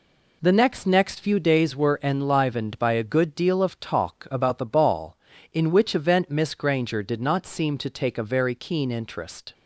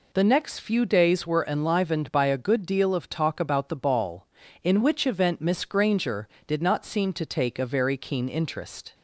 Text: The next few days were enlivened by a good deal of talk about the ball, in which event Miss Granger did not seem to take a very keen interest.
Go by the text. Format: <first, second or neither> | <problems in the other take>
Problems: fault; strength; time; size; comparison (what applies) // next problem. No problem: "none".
second | says "next" twice; at 0.8 s